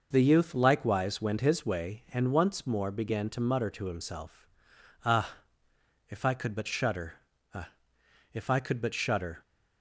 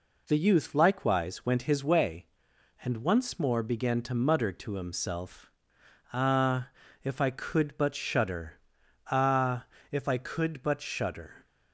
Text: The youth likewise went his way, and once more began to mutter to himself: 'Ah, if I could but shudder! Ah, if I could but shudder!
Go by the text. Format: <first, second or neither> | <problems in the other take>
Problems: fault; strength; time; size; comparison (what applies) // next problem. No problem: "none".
neither | none